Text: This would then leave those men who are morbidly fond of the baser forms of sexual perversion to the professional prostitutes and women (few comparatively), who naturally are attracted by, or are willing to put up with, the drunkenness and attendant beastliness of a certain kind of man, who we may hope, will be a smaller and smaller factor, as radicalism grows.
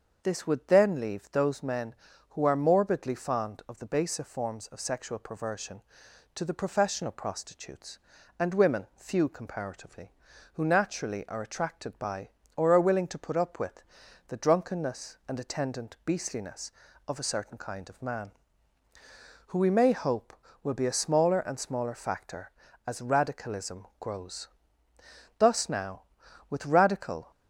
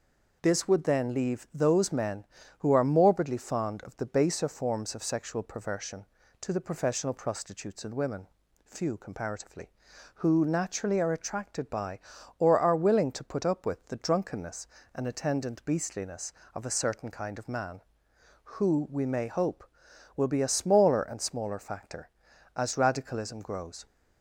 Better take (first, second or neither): second